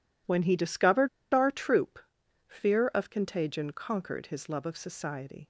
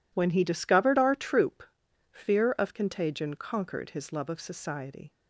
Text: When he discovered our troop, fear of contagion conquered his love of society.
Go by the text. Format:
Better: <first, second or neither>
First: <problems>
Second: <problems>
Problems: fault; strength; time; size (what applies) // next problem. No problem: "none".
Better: second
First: pauses between "discovered" and "our"; slight; at 1.0 s; 0.25 s long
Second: none